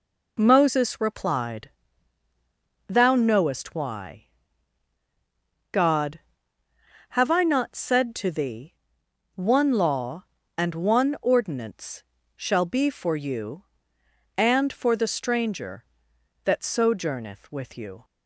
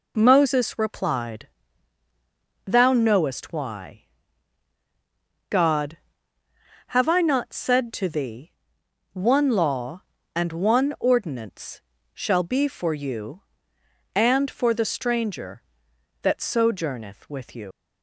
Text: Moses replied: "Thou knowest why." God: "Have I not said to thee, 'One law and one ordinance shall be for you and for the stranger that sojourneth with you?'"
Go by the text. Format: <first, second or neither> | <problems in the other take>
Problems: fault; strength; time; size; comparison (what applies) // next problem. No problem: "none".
first | pauses between "ordinance" and "shall"; slight; at 11.8 s; 0.32 s long; slight in the first // leaves "you" unfinished; at 17.7 s; 110 ms